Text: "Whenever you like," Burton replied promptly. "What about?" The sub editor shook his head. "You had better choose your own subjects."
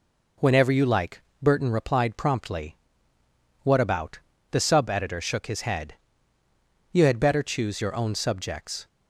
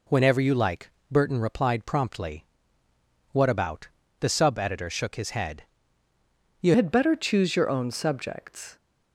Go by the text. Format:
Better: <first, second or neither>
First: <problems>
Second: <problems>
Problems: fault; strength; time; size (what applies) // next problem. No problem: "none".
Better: first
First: none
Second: changes voice at "had"; from 6.7 s on; 2.0 s long